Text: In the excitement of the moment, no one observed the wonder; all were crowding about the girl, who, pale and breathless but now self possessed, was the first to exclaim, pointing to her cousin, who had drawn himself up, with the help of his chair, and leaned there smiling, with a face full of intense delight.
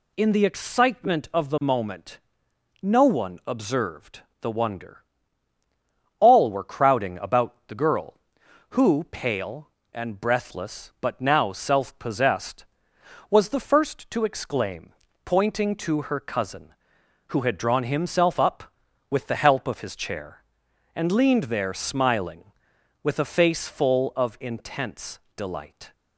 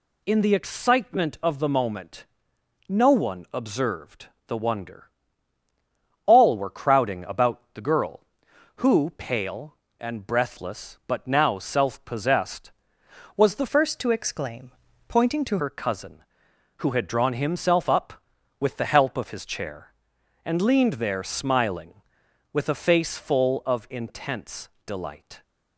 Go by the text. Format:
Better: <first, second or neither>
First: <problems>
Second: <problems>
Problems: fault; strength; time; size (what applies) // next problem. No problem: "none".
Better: first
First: pauses between "observed" and "the"; slight; at 4.2 s; 0.20 s long // pauses between "about" and "the"; slight; at 7.5 s; 0.16 s long // pauses between "intense" and "delight"; slight; at 25.1 s; 0.18 s long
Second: pauses between "observed" and "the"; slight; at 4.2 s; 0.20 s long // pauses between "about" and "the"; slight; at 7.5 s; 0.16 s long // changes voice from "first" to "to"; from 13.6 to 15.5 s; 1.9 s long // pauses between "intense" and "delight"; slight; at 24.6 s; 0.18 s long